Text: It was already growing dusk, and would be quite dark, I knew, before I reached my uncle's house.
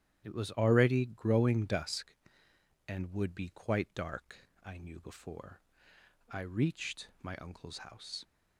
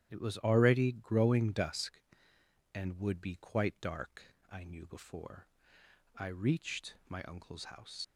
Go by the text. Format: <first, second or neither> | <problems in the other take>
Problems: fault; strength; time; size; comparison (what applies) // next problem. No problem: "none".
first | starts louder than the rest; strong; until 1.1 s; 10.5 dB; strong in the first // pauses between "before" and "I"; noticeable; at 5.4 s; 0.72 s long; noticeable in the first // leaves "house" unfinished; at 8.0 s; 50 ms